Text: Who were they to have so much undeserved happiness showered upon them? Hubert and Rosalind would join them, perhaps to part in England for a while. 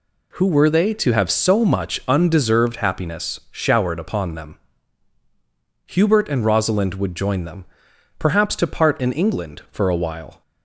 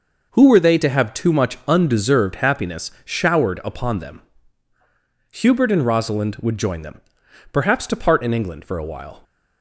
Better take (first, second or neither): first